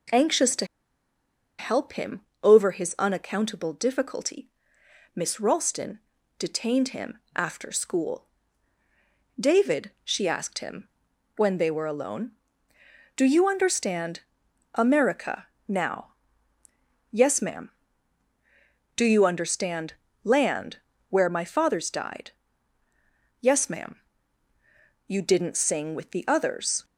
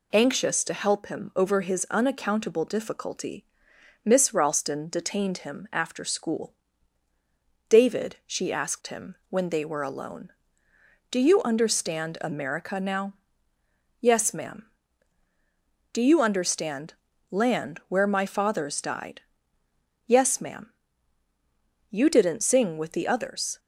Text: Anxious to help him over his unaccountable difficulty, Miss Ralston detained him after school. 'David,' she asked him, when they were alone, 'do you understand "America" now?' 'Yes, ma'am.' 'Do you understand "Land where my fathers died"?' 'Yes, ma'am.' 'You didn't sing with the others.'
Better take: second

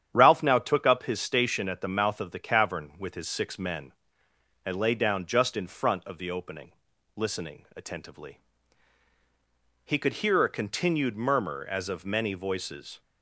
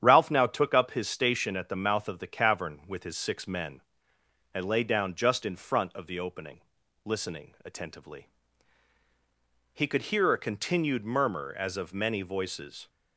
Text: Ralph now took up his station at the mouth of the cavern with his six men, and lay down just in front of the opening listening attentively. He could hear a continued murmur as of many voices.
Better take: neither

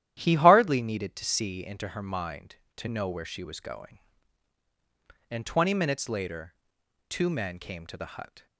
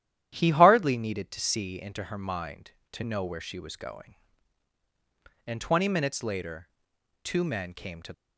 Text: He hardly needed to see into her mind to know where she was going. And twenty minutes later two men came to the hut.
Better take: first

